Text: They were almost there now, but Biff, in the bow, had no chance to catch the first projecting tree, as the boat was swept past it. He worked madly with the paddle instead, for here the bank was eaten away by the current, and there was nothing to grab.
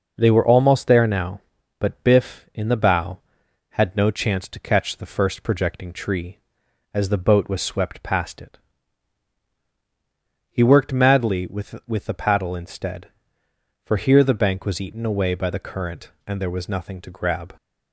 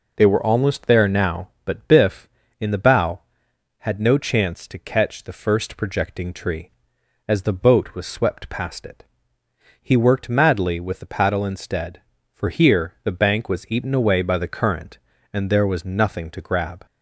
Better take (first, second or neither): second